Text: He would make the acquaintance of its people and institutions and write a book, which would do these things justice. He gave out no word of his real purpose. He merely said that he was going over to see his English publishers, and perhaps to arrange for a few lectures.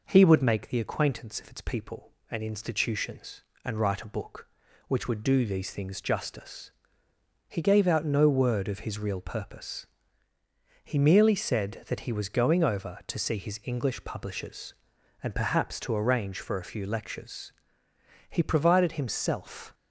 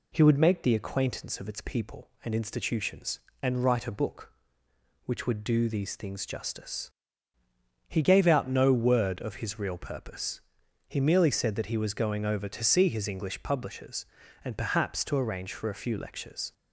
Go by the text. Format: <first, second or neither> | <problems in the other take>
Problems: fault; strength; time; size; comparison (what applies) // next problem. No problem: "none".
second | goes on to say "He provided himself"; from 18.2 s on; 1.4 s long